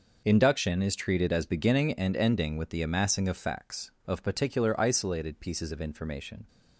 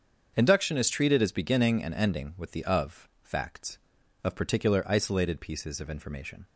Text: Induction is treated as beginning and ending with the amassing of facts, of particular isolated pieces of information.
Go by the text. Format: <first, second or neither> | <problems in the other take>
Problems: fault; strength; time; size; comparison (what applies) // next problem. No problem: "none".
first | starts louder than the rest; until 1.3 s; 7 dB // skips "amassing"; at 2.6 s